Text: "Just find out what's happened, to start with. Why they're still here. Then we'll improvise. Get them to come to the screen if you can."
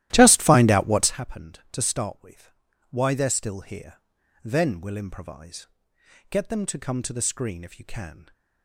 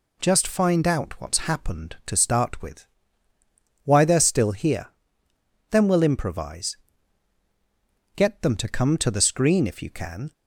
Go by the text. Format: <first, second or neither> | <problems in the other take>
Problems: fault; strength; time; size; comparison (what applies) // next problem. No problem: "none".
second | starts louder than the rest; strong; until 1.2 s; 14.5 dB